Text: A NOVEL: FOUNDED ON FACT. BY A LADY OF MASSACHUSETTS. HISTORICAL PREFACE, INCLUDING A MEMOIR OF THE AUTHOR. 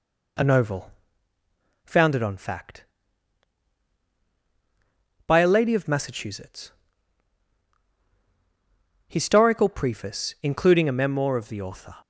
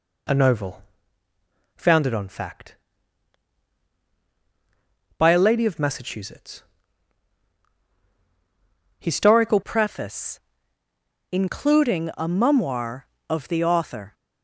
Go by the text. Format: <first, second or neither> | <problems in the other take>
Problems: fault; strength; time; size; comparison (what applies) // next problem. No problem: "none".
first | changes voice at "PREFACE"; from 9.6 s on; 4.5 s long